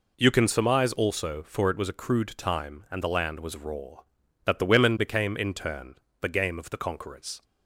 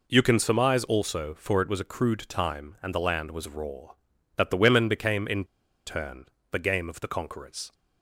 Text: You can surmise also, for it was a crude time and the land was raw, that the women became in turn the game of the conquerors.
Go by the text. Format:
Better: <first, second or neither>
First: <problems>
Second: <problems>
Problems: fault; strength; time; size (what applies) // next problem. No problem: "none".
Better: first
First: pauses between "turn" and "the"; slight; at 5.9 s; 0.26 s long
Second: pauses between "in" and "turn"; at 5.4 s; 0.42 s long // pauses between "turn" and "the"; slight; at 6.2 s; 0.26 s long